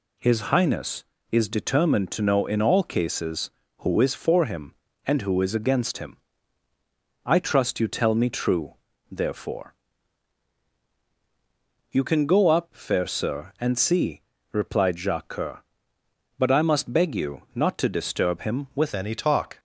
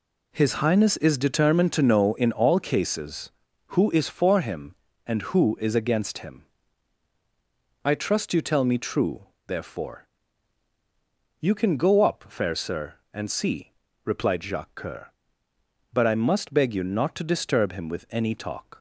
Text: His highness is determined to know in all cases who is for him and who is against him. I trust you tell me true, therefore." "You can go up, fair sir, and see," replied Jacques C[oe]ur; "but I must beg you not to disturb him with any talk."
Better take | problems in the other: second | changes voice at "any"; from 18.9 s on; 0.6 s long

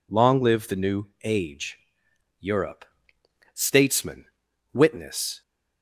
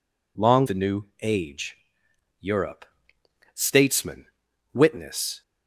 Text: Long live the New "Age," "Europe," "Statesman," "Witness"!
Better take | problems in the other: first | skips "live"; at 0.6 s // pauses between "New" and "Age"; slight; at 1.0 s; 0.16 s long; slight in the first

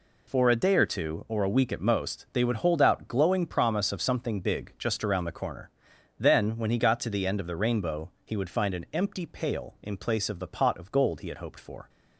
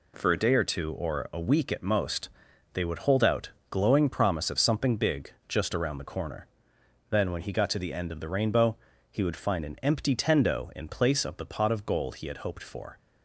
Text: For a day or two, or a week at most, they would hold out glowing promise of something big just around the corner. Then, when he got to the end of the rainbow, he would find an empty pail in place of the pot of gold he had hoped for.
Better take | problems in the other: first | pauses between "out" and "glowing"; slight; at 3.5 s; 0.18 s long // pauses between "big" and "just"; slight; at 5.3 s; 0.16 s long // says "tendo" for "pail"; at 10.1 s

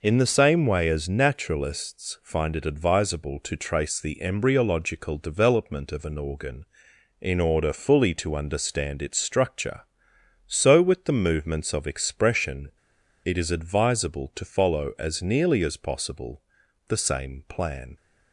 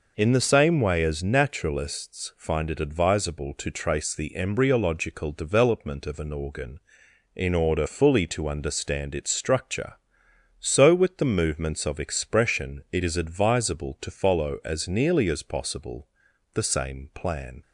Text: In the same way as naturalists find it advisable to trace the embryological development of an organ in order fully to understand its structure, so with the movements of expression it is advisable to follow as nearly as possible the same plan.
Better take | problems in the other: second | pauses between "expression" and "it"; noticeable; at 12.7 s; 0.55 s long // pauses between "possible" and "the"; noticeable; at 16.4 s; 0.48 s long; noticeable in the second

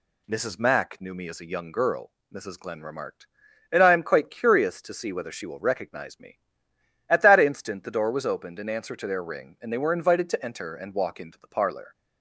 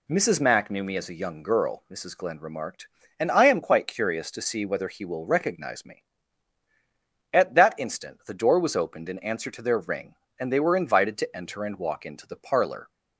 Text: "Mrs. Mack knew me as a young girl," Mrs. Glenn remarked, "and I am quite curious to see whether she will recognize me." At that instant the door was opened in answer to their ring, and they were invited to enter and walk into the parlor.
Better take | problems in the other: first | says "he" for "she"; at 4.8 s

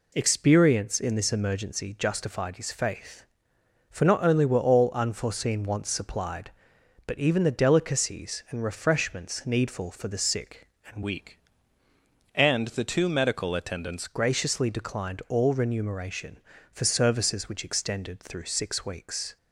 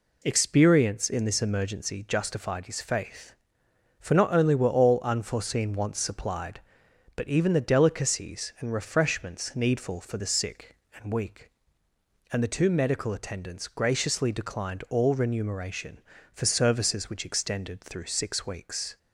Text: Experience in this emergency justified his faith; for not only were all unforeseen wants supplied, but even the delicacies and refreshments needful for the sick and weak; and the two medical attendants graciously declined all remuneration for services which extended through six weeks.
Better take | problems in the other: second | changes voice from "weak" to "attendants"; from 11.0 to 14.0 s; 3.0 s long

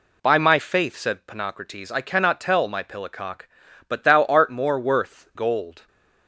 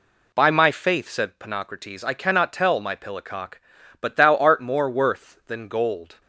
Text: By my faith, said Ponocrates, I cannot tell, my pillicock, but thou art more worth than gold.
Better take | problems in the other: second | skips "than"; at 5.3 s

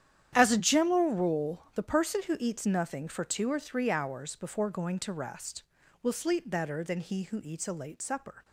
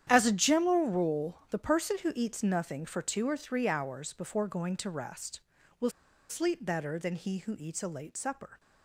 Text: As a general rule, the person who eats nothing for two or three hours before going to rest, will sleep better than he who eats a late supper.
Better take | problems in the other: first | starts louder than the rest; strong; until 1.1 s; 10 dB; strong in the first // pauses between "will" and "sleep"; at 5.9 s; 0.39 s long

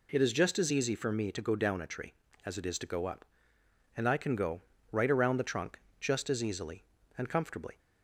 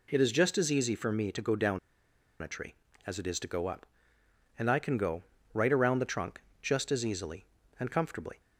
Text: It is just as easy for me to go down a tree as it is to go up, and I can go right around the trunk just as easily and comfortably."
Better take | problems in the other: first | pauses between "down" and "a"; noticeable; at 1.7 s; 0.63 s long // pauses between "go" and "right"; slight; at 5.2 s; 0.30 s long; slight in the first // pauses between "trunk" and "just"; slight; at 6.4 s; 0.22 s long; slight in the first

